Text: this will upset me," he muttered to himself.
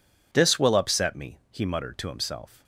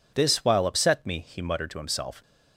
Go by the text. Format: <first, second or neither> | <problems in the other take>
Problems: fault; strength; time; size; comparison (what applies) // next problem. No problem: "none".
first | says "while" for "will"; at 0.4 s